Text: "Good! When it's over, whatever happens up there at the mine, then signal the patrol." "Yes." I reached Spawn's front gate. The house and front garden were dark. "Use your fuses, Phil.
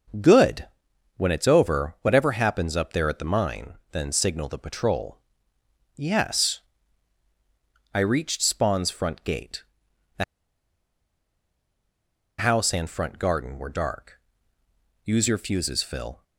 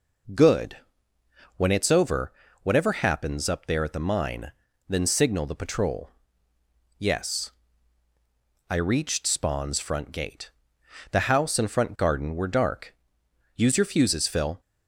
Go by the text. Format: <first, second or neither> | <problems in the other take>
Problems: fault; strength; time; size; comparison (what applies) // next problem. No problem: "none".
second | starts louder than the rest; until 1.7 s; 6.5 dB // pauses between "The" and "house"; strong; at 10.2 s; 2.1 s long